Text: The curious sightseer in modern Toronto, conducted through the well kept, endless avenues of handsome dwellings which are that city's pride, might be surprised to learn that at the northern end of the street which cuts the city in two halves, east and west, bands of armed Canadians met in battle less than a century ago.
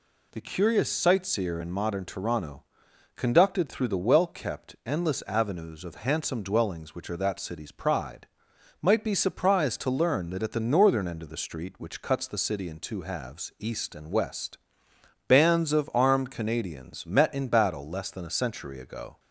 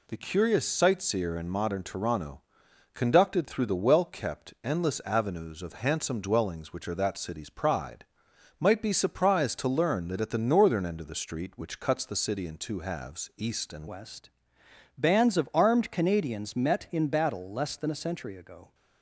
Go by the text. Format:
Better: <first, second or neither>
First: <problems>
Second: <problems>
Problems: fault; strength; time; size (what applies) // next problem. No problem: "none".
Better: first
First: none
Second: changes voice at "west"; from 13.8 s on; 4.9 s long